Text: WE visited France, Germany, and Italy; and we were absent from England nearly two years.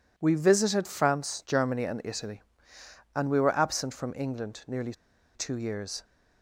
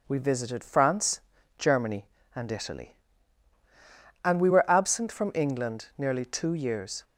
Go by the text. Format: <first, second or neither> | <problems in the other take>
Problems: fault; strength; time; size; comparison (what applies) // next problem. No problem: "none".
second | pauses between "nearly" and "two"; at 4.9 s; 0.40 s long